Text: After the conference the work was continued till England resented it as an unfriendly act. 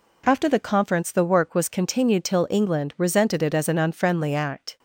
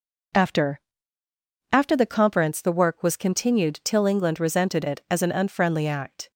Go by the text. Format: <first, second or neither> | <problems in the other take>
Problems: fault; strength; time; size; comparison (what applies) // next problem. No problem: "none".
first | says "After" twice; at 1.7 s